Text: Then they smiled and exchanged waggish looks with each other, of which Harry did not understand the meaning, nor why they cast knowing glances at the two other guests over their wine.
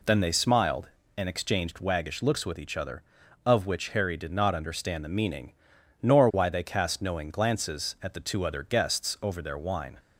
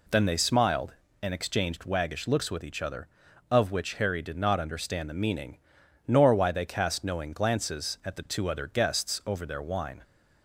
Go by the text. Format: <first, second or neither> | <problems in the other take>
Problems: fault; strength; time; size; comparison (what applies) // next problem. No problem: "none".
neither | none